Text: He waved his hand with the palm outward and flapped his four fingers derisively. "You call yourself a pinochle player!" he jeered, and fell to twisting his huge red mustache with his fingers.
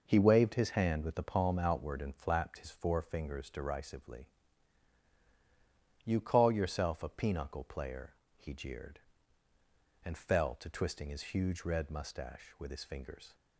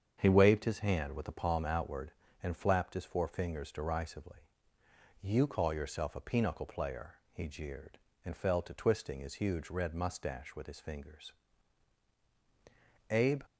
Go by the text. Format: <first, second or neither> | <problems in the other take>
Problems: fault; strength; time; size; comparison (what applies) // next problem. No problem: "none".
first | starts louder than the rest; strong; until 1.1 s; 7.5 dB // goes on to say "Abe"; slight; from 13.0 s on; 0.34 s long